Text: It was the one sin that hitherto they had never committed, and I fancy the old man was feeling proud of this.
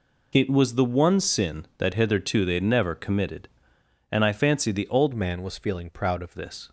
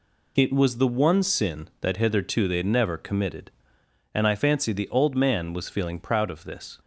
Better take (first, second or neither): second